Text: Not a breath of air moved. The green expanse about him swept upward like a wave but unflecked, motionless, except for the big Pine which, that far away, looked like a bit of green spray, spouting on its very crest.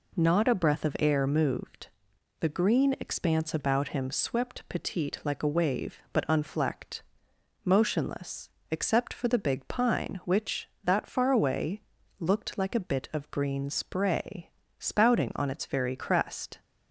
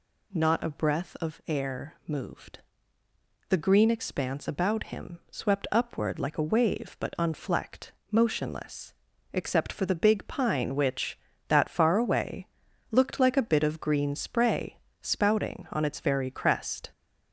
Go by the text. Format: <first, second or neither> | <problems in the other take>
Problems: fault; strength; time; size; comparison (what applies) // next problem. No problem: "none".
second | says "petite" for "upward"; at 4.6 s